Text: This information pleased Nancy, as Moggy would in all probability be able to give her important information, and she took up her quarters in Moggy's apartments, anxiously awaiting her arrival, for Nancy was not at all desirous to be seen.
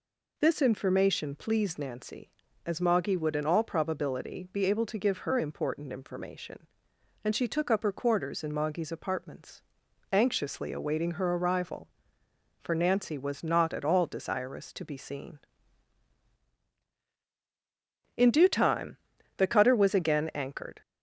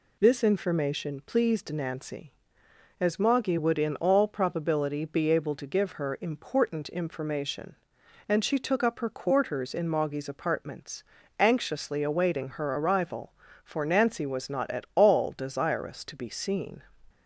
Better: second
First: goes on to say "In due time the cutter was again anchored"; strong; from 18.1 s on; 2.6 s long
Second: none

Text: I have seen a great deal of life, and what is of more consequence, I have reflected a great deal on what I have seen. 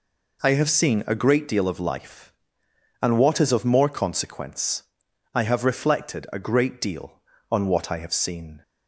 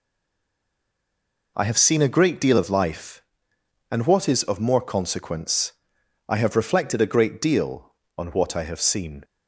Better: first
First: none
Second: stays silent before the first word; noticeable; until 1.5 s; 1.5 s long

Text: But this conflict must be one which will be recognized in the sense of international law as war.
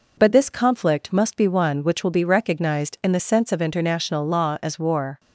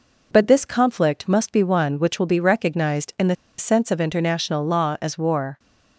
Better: first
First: none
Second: pauses between "the" and "sense"; slight; at 3.3 s; 0.23 s long

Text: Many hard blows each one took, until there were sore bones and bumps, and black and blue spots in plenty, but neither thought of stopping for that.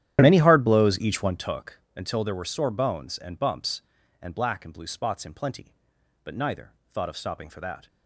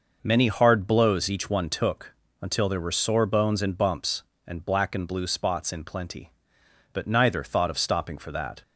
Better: second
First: starts louder than the rest; strong; until 1.5 s; 11 dB // pauses between "neither" and "thought"; slight; at 6.7 s; 0.18 s long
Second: none

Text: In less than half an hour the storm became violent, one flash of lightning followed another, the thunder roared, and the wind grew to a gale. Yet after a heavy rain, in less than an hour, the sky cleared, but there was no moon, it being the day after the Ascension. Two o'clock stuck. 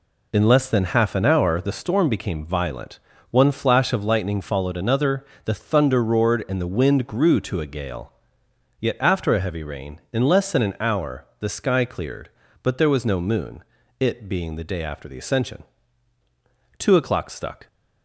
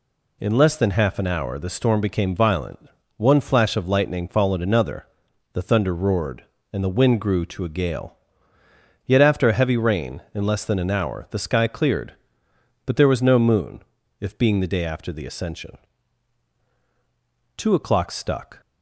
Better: first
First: none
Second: says "if" for "it"; at 14.2 s

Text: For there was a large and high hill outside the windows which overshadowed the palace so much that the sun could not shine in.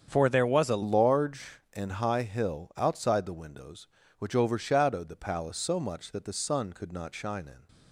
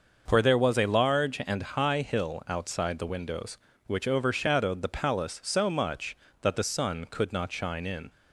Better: second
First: starts louder than the rest; strong; until 1.0 s; 7.5 dB // changes voice at "large"; from 0.8 s on; 6.8 s long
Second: starts louder than the rest; noticeable; until 1.2 s; 6 dB

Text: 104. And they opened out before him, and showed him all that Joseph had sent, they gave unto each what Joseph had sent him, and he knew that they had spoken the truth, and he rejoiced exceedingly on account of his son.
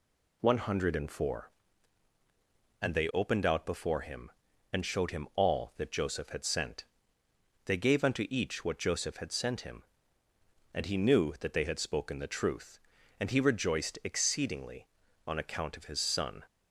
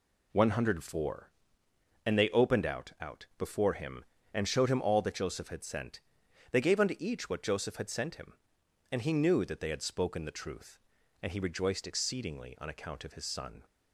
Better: first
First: none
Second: says "out" twice; at 2.9 s

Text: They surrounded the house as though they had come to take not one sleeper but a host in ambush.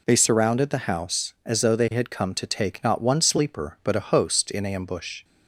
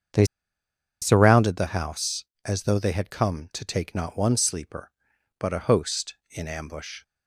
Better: first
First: none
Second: starts louder than the rest; until 1.9 s; 7 dB // pauses between "They" and "surrounded"; noticeable; at 0.2 s; 0.77 s long

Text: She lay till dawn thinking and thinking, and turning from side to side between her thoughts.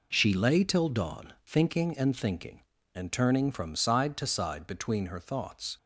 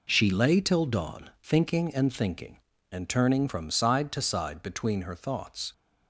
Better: neither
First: none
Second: none

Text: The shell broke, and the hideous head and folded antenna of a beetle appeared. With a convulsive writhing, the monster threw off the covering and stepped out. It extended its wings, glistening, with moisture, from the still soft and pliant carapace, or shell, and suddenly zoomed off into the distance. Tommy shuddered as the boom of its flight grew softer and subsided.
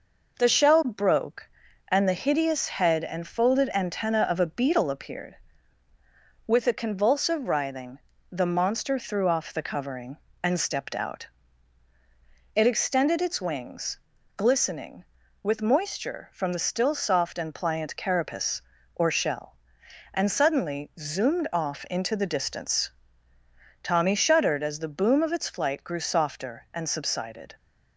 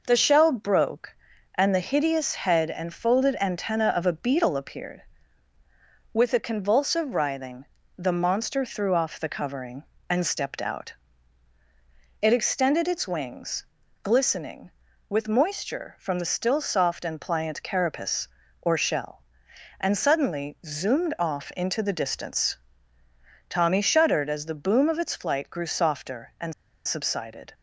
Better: first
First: none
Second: pauses between "and" and "subsided"; slight; at 26.5 s; 0.34 s long

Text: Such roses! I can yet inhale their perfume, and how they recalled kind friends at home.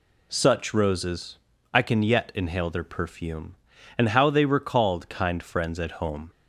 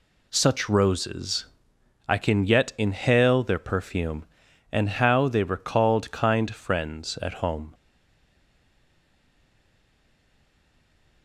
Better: first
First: none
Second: stays silent after the last word; strong; from 7.7 s on; 3.5 s long

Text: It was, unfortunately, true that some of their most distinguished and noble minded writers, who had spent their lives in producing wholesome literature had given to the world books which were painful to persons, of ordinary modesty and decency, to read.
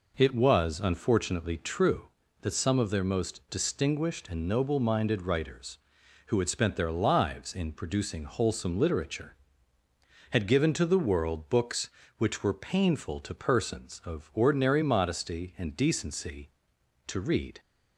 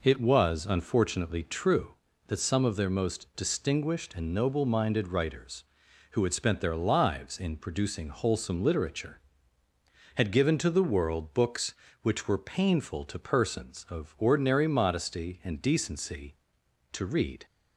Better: neither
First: none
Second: none

